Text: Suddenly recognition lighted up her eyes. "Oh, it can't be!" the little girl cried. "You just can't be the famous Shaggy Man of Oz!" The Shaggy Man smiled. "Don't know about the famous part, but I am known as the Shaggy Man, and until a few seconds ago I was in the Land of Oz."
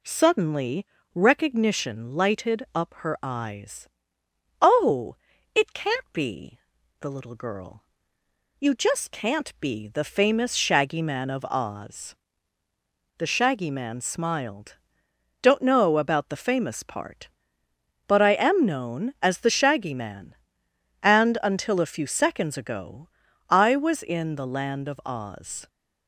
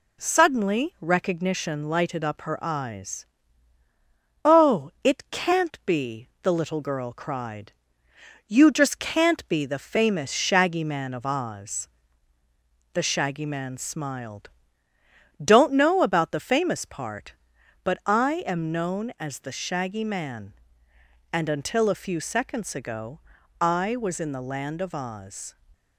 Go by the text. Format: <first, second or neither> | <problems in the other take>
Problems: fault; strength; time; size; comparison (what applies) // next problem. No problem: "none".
second | pauses between "Suddenly" and "recognition"; slight; at 0.8 s; 0.28 s long // skips "cried"; at 8.2 s // pauses between "ago" and "I"; at 23.0 s; 0.42 s long; also in the second